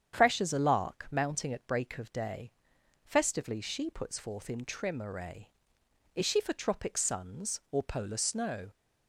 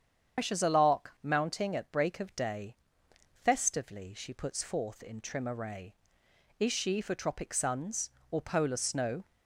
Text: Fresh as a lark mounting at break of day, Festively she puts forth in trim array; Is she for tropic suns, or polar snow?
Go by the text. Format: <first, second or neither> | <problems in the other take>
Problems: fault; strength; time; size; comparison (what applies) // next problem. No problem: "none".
first | loses the start of "Fresh"; at 0.3 s; 150 ms // starts louder than the rest; strong; until 1.4 s; 8 dB; strong in the first